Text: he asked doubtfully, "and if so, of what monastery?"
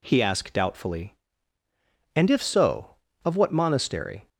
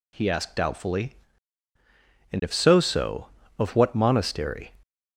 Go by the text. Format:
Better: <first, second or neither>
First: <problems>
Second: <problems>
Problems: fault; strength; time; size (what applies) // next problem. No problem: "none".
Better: first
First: none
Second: says "so" twice; at 2.8 s